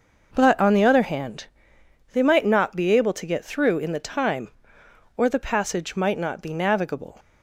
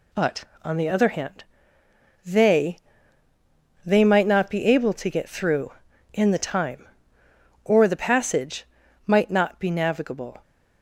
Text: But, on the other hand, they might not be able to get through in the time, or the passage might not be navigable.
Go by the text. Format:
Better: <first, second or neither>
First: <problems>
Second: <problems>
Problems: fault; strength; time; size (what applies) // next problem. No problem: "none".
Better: first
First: none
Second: says "they" twice; at 3.8 s // pauses between "passage" and "might"; at 8.6 s; 0.40 s long